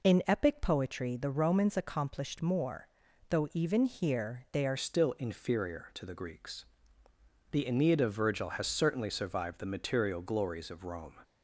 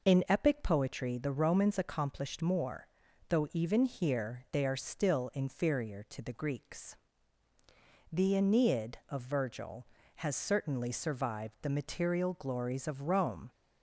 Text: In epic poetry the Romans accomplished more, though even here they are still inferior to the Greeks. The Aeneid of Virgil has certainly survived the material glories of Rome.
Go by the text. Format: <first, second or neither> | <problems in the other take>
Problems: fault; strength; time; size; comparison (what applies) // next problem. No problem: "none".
second | changes voice at "still"; from 4.7 s on; 6.4 s long